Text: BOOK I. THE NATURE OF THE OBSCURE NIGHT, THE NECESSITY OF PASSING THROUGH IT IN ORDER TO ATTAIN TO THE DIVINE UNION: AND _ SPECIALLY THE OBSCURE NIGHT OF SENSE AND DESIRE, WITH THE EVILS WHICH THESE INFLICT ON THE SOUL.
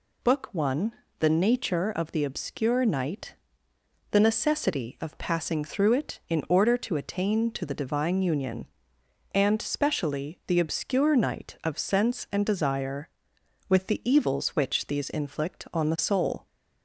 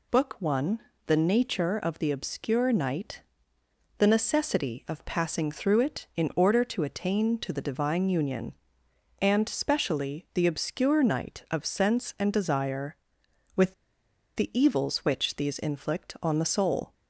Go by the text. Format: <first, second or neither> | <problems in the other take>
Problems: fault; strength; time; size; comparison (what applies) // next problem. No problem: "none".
first | pauses between "WITH" and "THE"; noticeable; at 13.7 s; 0.62 s long